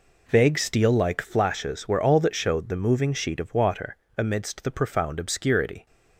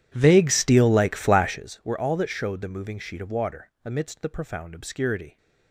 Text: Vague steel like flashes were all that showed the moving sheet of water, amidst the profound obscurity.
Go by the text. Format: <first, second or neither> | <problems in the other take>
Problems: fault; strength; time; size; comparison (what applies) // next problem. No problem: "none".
first | starts louder than the rest; strong; until 1.6 s; 11.5 dB